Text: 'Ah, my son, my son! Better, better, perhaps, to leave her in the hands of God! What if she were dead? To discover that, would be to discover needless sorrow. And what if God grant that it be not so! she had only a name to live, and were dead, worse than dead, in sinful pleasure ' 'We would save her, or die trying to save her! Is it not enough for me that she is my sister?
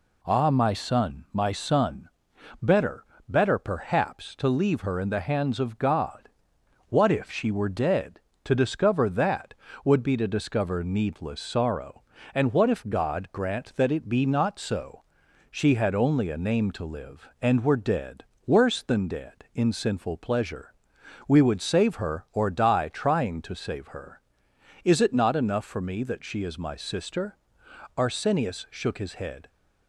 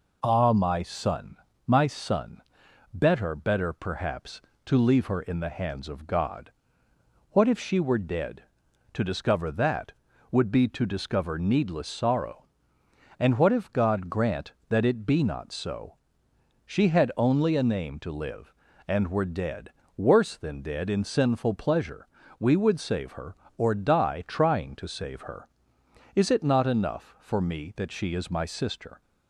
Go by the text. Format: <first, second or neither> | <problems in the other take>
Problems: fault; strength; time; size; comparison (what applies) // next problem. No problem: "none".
second | goes on to say "Arsenius shook his head"; from 27.9 s on; 1.5 s long